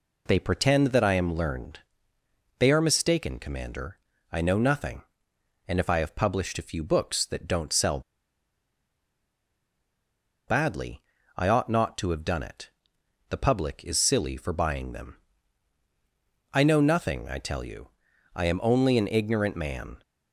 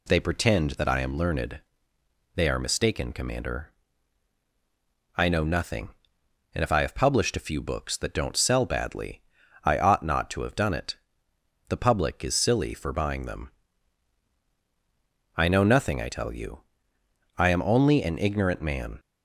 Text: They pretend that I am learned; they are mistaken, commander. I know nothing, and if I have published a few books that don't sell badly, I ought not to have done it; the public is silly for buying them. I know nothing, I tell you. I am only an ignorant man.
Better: second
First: pauses between "sell" and "badly"; strong; at 8.0 s; 2.4 s long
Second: none

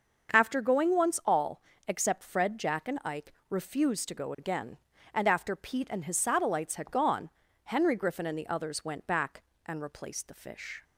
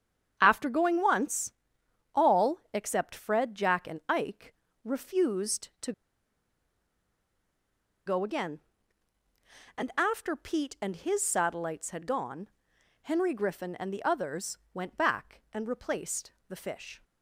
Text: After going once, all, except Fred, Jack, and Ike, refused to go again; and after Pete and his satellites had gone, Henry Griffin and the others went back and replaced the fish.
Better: first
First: starts louder than the rest; until 1.3 s; 6.5 dB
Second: starts louder than the rest; strong; until 1.4 s; 8.5 dB // pauses between "to" and "go"; strong; at 5.9 s; 2.1 s long // pauses between "others" and "went"; slight; at 14.5 s; 0.16 s long // pauses between "replaced" and "the"; slight; at 16.3 s; 0.16 s long

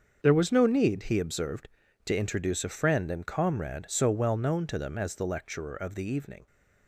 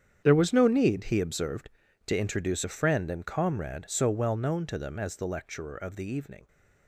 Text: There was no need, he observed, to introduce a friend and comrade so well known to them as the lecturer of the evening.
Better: first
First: starts louder than the rest; until 1.2 s; 6.5 dB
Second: gets quieter; strong; throughout; 14 dB // starts louder than the rest; strong; until 1.2 s; 8.5 dB

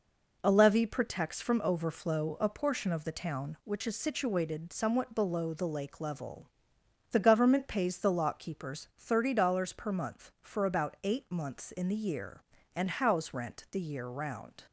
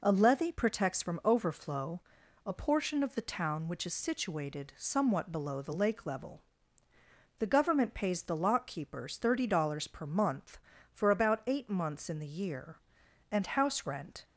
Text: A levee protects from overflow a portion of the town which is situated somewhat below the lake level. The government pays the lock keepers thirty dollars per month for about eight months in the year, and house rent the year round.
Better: first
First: none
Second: pauses between "overflow" and "a"; noticeable; at 2.0 s; 0.46 s long // stops before "the year round"; at 14.2 s

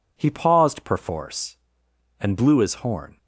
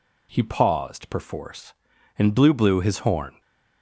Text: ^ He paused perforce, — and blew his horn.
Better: first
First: none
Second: says "blew" twice; at 2.5 s // stays silent after the last word; slight; from 3.3 s on; 0.5 s long

